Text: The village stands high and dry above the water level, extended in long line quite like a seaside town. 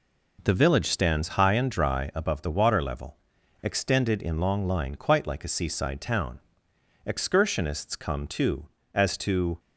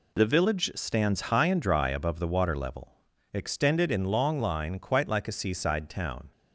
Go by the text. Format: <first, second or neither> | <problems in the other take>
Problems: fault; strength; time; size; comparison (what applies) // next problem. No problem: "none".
second | goes on to say "Excursionists come too as to"; strong; from 7.0 s on; 2.5 s long